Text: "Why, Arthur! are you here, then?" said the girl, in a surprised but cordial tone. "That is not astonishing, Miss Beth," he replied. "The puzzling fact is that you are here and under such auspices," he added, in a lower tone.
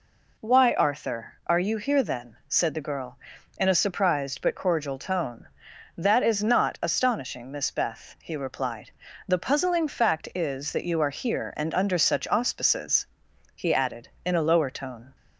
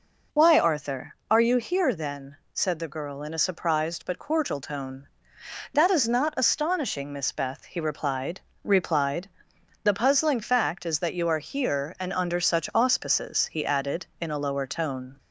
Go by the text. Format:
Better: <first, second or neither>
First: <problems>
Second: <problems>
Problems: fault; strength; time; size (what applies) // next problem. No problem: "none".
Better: first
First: none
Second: says "replied" twice; at 8.6 s